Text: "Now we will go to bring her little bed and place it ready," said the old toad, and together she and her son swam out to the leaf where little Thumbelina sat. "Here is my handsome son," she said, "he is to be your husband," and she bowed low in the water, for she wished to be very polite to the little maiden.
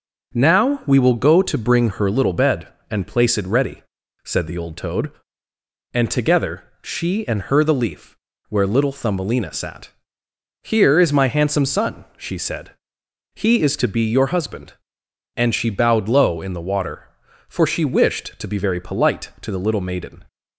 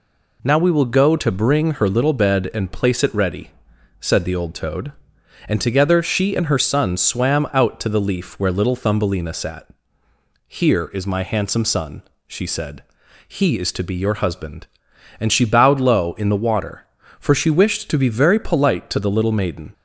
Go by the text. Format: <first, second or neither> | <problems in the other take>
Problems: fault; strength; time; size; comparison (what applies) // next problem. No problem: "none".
second | pauses between "together" and "she"; slight; at 6.6 s; 0.16 s long // skips "son swam out to"; at 7.6 s // pauses between "leaf" and "where"; slight; at 8.1 s; 0.32 s long